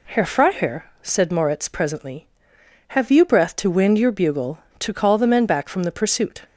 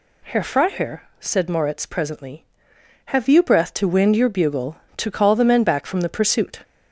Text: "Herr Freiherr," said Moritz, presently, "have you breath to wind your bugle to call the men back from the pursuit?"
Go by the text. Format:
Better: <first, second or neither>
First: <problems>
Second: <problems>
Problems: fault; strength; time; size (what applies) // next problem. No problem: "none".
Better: first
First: none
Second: gets louder; slight; throughout; 3 dB